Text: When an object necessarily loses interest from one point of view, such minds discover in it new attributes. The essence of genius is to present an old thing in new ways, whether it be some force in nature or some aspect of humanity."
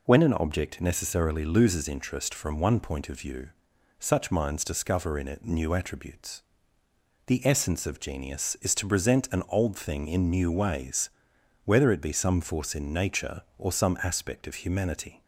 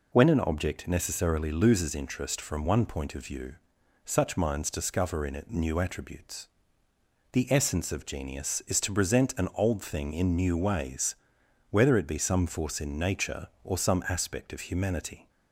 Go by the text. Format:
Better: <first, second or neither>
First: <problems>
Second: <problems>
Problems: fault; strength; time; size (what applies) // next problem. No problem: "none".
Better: neither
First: none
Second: none